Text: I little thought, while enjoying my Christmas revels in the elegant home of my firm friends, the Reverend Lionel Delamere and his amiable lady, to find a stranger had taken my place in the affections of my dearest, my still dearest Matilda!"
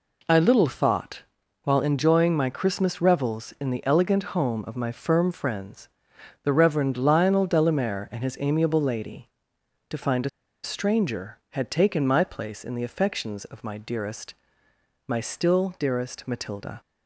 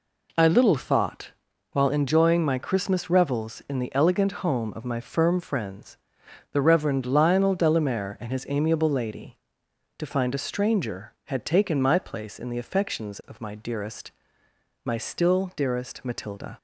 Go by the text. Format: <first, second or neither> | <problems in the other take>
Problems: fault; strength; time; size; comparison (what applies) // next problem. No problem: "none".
second | pauses between "a" and "stranger"; at 10.2 s; 0.36 s long